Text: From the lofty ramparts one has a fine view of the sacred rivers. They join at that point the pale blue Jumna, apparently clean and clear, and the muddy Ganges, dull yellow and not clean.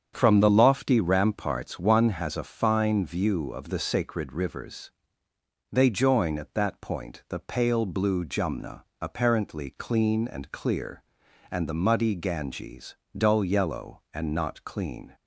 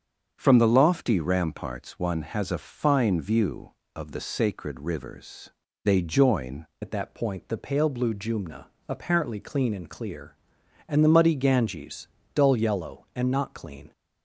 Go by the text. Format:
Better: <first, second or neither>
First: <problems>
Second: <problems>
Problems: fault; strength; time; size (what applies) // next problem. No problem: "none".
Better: first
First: starts louder than the rest; strong; until 1.1 s; 8 dB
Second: starts louder than the rest; until 1.3 s; 7 dB // changes voice at "at"; from 6.8 s on; 7.1 s long